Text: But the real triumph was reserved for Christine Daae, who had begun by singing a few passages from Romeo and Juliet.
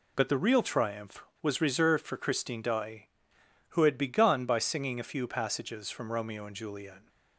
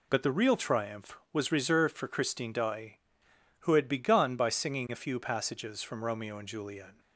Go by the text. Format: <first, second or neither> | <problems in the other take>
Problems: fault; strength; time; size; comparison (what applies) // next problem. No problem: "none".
neither | none